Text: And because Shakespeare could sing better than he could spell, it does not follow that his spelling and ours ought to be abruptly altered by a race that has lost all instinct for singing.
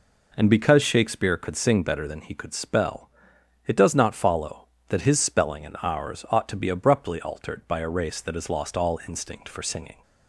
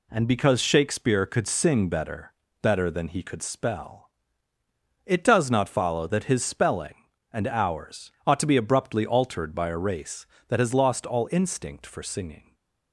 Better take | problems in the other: first | says "better" twice; at 2.6 s // pauses between "ours" and "ought"; slight; at 8.0 s; 0.16 s long // stays silent after the last word; slight; from 12.3 s on; 0.6 s long

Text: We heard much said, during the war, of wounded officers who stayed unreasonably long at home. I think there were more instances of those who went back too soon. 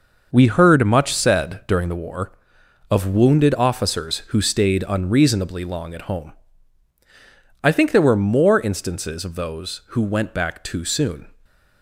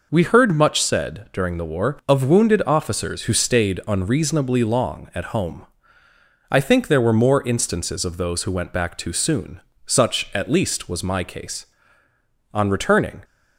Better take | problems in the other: first | goes on to say "Such at least was my case On returning"; strong; from 9.8 s on; 3.3 s long

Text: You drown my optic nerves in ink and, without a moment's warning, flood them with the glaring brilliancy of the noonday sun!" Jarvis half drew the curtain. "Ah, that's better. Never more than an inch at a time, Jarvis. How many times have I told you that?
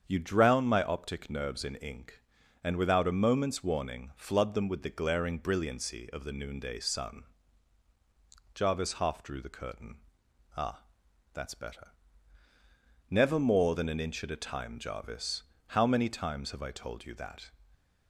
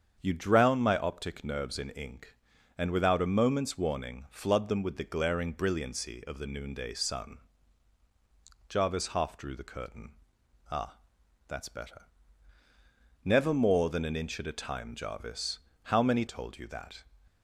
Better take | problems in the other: first | starts louder than the rest; strong; until 1.2 s; 7.5 dB; strong in the first // skips "times have I"; at 16.2 s

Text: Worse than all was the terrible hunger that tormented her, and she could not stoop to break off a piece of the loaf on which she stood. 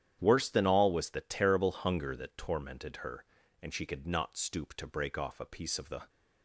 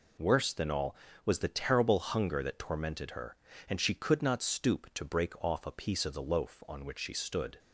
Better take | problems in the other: second | starts louder than the rest; strong; until 1.2 s; 10 dB // stops before "loaf on which she stood"; at 6.0 s

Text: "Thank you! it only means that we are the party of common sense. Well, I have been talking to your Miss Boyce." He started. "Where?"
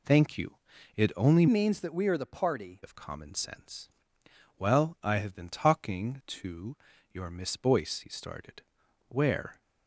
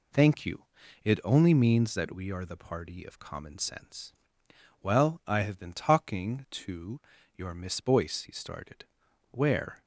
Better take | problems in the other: second | changes voice from "means" to "party"; from 1.4 to 2.8 s; 1.4 s long // pauses between "to" and "your"; at 6.7 s; 0.38 s long; also in the second

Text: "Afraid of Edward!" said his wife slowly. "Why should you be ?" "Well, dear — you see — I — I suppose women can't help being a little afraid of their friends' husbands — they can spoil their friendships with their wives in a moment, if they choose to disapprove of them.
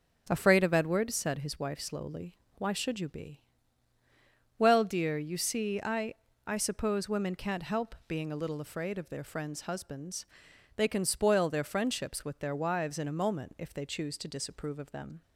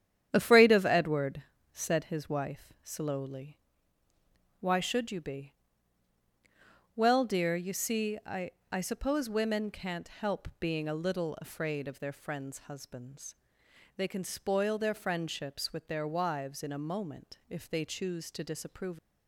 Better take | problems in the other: first | starts louder than the rest; strong; until 1.3 s; 10 dB // stops before "of them"; at 18.9 s

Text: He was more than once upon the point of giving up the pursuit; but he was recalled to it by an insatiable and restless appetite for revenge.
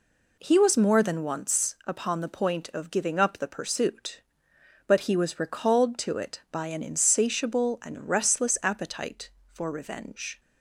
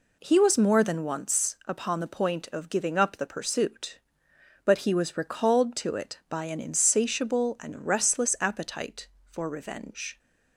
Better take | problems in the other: neither | none

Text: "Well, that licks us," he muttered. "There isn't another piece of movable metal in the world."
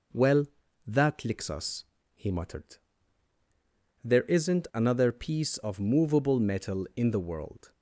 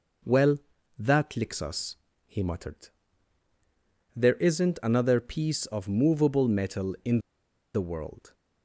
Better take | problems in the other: first | pauses between "in" and "the"; noticeable; at 7.1 s; 0.56 s long

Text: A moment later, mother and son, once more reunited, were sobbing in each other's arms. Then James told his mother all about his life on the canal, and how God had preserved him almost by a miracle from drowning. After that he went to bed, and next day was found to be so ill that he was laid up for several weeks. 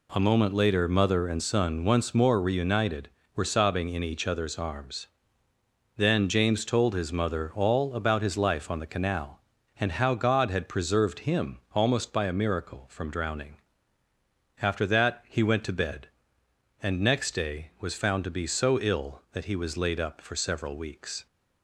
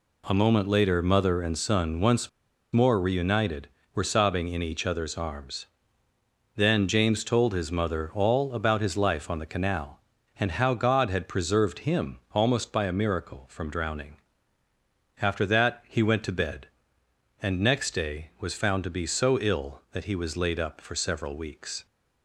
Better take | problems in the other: first | pauses between "once" and "more"; at 2.2 s; 0.44 s long // pauses between "him" and "almost"; slight; at 12.1 s; 0.16 s long; slight in the first

